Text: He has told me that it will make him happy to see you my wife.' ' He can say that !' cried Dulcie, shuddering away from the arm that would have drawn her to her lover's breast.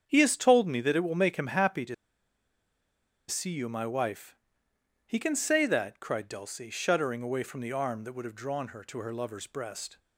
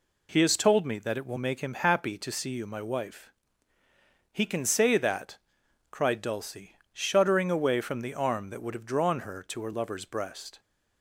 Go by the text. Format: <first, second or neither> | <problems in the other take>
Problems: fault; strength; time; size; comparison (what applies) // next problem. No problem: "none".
second | starts louder than the rest; strong; until 1.0 s; 7.5 dB // pauses between "to" and "see"; strong; at 1.9 s; 1.3 s long